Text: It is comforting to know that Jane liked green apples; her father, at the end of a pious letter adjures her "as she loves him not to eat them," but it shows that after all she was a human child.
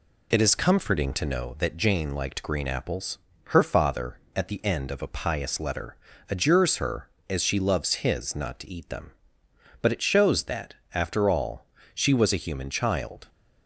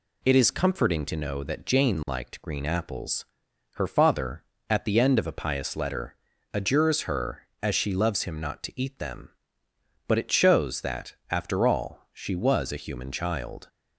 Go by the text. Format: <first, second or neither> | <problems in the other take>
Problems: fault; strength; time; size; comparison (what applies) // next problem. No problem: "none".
second | pauses between "letter" and "adjures"; slight; at 5.9 s; 0.32 s long; slight in the second // says "his" for "him"; at 7.9 s // pauses between "that" and "after"; slight; at 10.7 s; 0.18 s long; slight in the second // pauses between "all" and "she"; slight; at 11.6 s; 0.30 s long